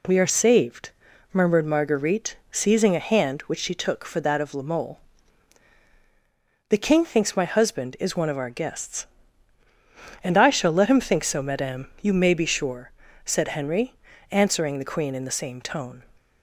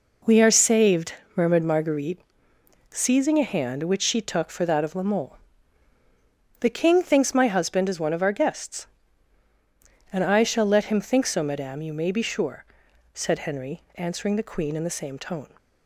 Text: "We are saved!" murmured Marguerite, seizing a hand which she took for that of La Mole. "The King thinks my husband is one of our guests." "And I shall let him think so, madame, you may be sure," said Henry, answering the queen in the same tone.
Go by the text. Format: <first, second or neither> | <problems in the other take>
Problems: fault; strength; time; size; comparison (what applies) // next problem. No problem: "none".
neither | none